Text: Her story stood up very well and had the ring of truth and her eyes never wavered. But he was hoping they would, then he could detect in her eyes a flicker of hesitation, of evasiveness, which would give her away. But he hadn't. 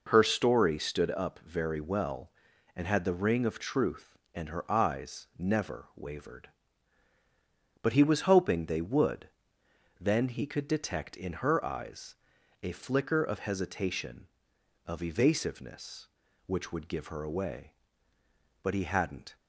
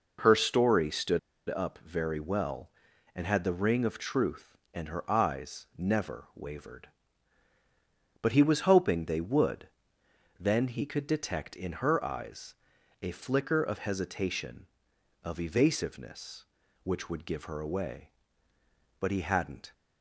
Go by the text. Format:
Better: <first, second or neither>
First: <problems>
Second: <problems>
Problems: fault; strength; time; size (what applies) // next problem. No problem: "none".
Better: first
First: pauses between "eyes" and "a"; noticeable; at 12.1 s; 0.48 s long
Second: pauses between "stood" and "up"; slight; at 1.1 s; 0.29 s long // pauses between "eyes" and "a"; noticeable; at 12.5 s; 0.48 s long